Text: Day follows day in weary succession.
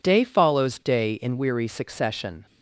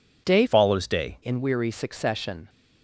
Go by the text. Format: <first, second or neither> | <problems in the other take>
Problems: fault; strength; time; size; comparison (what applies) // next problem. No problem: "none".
first | changes voice from "follows" to "day"; from 0.4 to 1.1 s; 0.7 s long